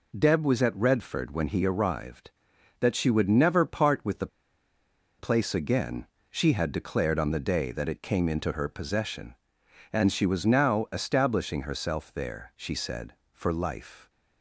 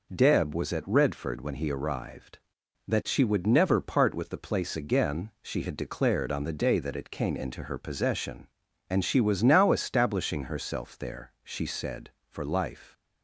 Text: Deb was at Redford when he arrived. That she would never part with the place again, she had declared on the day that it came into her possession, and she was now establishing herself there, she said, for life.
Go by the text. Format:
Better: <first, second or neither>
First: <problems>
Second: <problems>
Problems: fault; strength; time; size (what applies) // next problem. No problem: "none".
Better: second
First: pauses between "the" and "place"; noticeable; at 4.2 s; 0.92 s long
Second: none